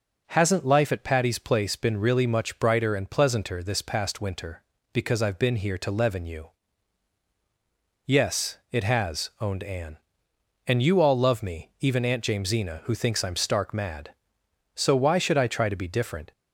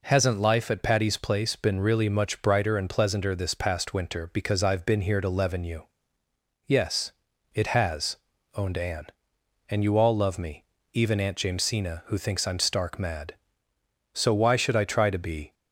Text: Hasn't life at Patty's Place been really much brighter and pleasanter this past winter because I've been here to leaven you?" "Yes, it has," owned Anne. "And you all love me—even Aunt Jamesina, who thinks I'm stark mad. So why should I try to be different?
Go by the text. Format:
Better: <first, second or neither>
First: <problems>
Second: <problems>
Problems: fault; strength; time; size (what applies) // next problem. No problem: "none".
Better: first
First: none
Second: stops before "different"; at 15.5 s